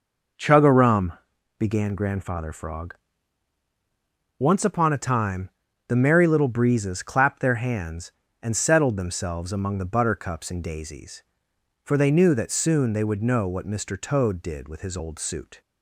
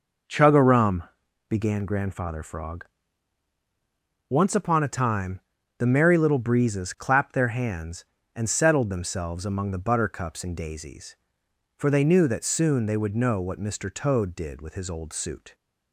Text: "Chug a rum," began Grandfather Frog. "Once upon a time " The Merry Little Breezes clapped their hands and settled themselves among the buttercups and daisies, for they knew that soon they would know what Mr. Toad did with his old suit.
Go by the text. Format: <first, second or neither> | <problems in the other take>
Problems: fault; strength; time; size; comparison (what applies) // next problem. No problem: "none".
neither | none